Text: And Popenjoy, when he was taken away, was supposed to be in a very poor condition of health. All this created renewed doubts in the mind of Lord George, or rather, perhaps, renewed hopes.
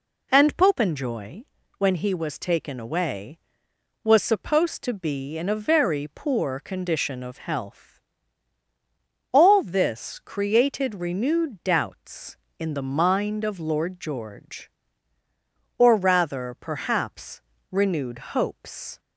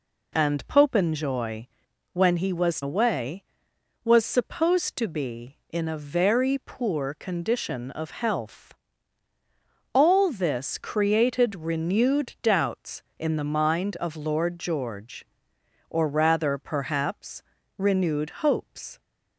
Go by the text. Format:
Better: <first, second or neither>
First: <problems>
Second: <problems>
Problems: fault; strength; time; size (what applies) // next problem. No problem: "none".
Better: first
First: none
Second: skips "taken"; at 2.8 s